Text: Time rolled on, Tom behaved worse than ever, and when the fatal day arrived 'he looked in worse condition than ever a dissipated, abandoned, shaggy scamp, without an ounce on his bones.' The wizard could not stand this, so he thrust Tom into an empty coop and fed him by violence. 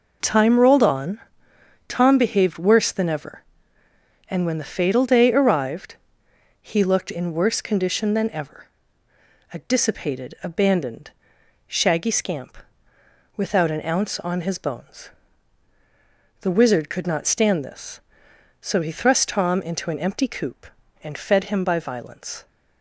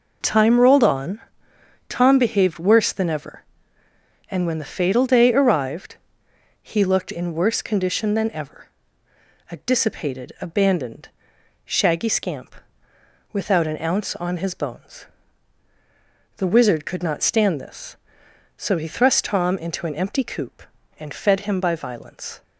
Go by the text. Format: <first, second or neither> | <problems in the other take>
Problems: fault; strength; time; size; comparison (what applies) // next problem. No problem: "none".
neither | pauses between "arrived" and "he"; noticeable; the same in both // pauses between "ever" and "a"; noticeable; the same in both